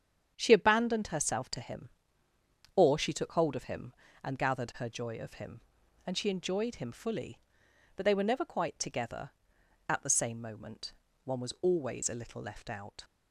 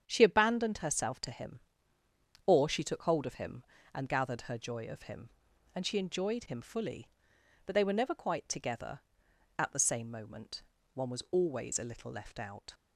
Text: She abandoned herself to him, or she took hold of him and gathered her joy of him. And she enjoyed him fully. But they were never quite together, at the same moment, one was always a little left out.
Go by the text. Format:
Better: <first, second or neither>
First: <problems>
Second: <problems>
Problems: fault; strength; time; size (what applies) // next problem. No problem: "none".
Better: neither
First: starts louder than the rest; strong; until 1.3 s; 8 dB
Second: starts louder than the rest; strong; until 1.0 s; 8 dB